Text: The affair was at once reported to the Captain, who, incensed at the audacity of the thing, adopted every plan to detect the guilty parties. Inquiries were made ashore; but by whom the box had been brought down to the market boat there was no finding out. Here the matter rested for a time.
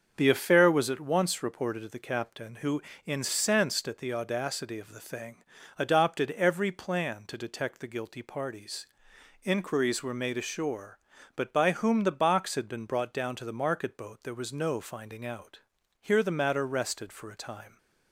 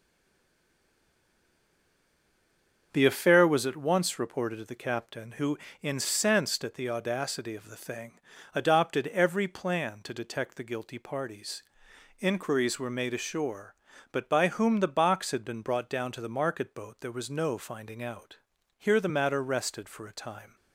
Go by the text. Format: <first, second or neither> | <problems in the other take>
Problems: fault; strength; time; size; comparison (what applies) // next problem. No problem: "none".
first | stays silent before the first word; strong; until 2.9 s; 2.9 s long // starts louder than the rest; until 3.9 s; 6.5 dB; also in the first